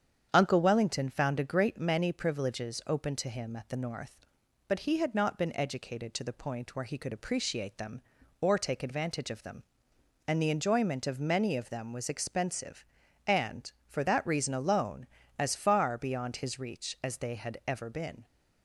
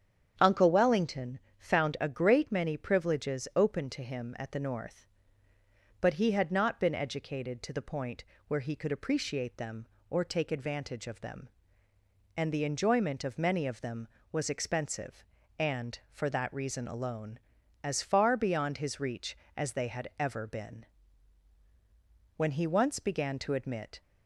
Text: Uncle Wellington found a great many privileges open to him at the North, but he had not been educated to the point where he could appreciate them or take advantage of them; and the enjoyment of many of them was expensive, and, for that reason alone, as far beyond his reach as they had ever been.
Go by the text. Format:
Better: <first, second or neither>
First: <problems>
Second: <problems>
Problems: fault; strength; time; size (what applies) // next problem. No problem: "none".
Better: first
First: starts louder than the rest; strong; until 1.3 s; 8.5 dB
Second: starts louder than the rest; strong; until 1.6 s; 8.5 dB // pauses between "Wellington" and "found"; slight; at 1.3 s; 0.20 s long // pauses between "point" and "where"; slight; at 8.2 s; 0.24 s long // goes on to say "When he once began to admit"; from 22.3 s on; 1.6 s long